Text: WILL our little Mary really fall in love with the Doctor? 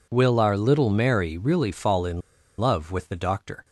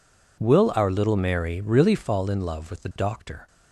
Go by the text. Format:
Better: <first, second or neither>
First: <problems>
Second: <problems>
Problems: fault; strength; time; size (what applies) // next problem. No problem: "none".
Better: second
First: pauses between "in" and "love"; at 2.2 s; 0.37 s long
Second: none